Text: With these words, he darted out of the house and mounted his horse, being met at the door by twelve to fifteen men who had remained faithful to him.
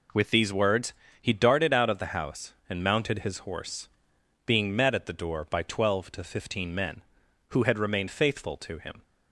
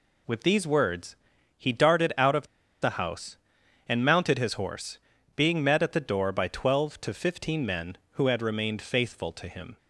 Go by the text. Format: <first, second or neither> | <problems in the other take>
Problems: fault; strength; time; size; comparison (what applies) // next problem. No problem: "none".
first | pauses between "of" and "the"; slight; at 2.4 s; 0.35 s long